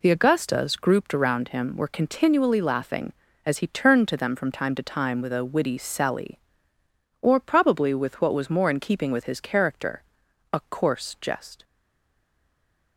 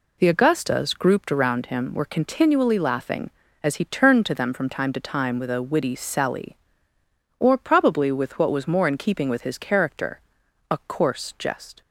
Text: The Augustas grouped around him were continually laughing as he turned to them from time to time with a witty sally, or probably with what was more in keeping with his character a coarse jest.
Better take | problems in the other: second | pauses between "character" and "a"; noticeable; at 10.0 s; 0.50 s long; noticeable in the second // stays silent after the last word; noticeable; from 11.6 s on; 1.3 s long

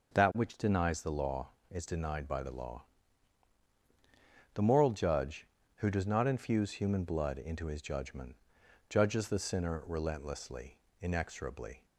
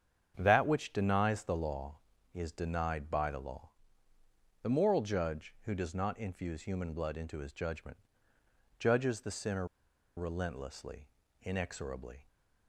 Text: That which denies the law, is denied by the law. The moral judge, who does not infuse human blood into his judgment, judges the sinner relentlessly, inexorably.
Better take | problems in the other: first | starts louder than the rest; strong; until 1.3 s; 8 dB // pauses between "sinner" and "relentlessly"; noticeable; at 9.6 s; 0.51 s long

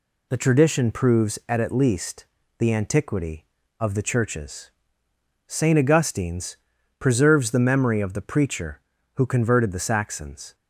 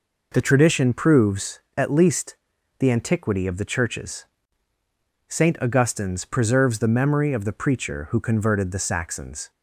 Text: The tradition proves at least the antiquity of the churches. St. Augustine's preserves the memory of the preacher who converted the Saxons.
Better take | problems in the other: second | says "at" twice; at 1.6 s // pauses between "least" and "the"; slight; at 2.2 s; 0.33 s long; also in the second // pauses between "Augustine's" and "preserves"; at 6.5 s; 0.42 s long

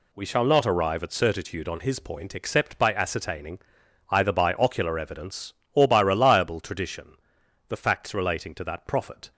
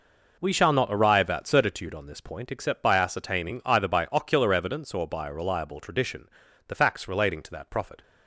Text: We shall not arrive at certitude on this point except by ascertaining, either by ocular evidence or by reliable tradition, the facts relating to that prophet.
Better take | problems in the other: second | says "his" for "this"; at 1.7 s

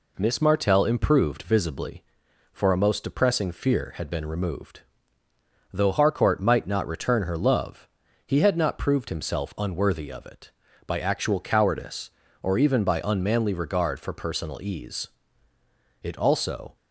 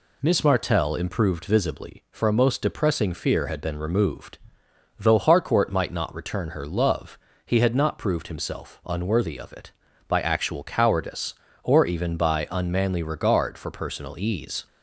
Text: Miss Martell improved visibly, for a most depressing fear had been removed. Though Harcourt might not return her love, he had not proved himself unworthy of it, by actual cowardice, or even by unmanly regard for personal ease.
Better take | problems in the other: second | goes on to say "It also"; noticeable; from 16.0 s on; 0.74 s long

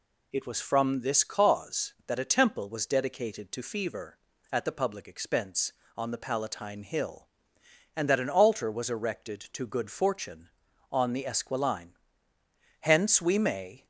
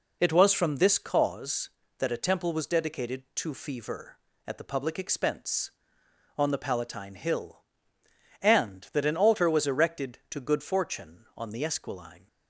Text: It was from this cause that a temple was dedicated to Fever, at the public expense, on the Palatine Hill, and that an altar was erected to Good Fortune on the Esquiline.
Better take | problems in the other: second | goes on to say "Hence we may"; noticeable; from 12.8 s on; 1.0 s long

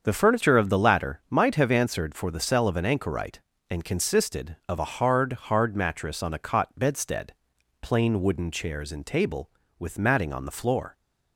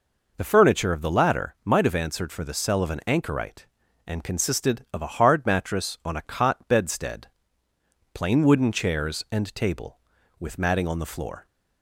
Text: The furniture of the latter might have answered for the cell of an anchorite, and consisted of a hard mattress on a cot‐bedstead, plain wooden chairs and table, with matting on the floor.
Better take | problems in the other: second | starts louder than the rest; until 1.0 s; 7 dB // says "hard" twice; at 5.3 s

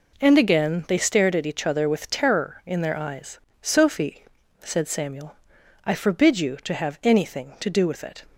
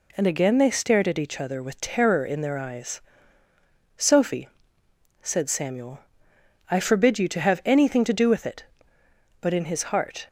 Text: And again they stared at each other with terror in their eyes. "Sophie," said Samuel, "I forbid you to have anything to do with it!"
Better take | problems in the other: first | goes on to say "But in his heart"; noticeable; from 9.3 s on; 0.88 s long

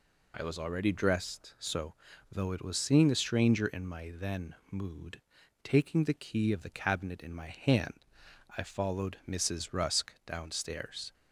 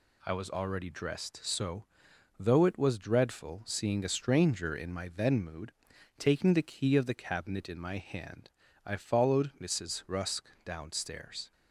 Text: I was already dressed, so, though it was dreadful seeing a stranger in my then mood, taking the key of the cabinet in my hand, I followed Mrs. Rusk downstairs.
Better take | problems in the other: second | skips "dreadful"; at 2.7 s // pauses between "then" and "mood"; slight; at 4.5 s; 0.16 s long

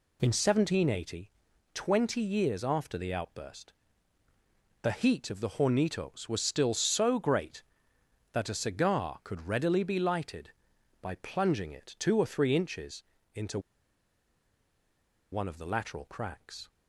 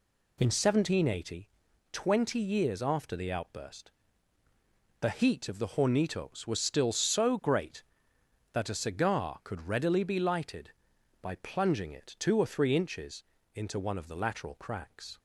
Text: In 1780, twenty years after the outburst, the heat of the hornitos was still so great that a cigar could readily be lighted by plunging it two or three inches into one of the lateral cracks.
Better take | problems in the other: second | pauses between "inches" and "into"; slight; at 13.0 s; 0.30 s long; slight in the second // pauses between "into" and "one"; strong; at 13.5 s; 1.7 s long

